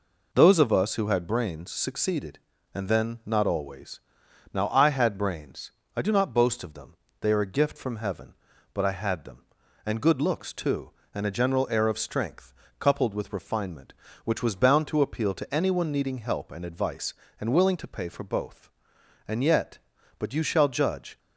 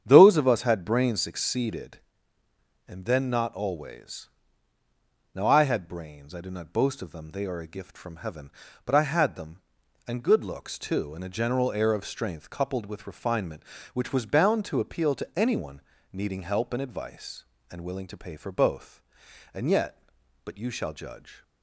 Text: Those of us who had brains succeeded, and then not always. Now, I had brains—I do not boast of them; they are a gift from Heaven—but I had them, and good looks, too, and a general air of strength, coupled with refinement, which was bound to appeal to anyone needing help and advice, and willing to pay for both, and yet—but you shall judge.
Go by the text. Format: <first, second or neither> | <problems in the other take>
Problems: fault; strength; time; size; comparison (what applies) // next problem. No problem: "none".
first | starts louder than the rest; strong; until 1.0 s; 8.5 dB // skips "who"; at 0.6 s // pauses between "anyone" and "needing"; slight; at 15.8 s; 0.32 s long